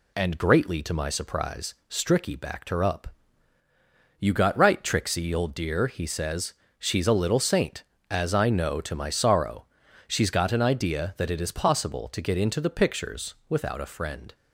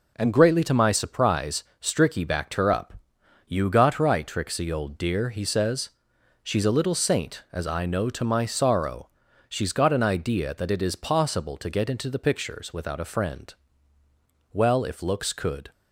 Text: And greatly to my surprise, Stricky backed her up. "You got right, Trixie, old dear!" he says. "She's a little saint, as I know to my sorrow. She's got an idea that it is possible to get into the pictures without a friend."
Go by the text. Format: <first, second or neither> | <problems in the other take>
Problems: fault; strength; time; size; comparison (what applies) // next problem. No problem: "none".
first | goes on to say "Well if looks could"; noticeable; from 14.5 s on; 1.1 s long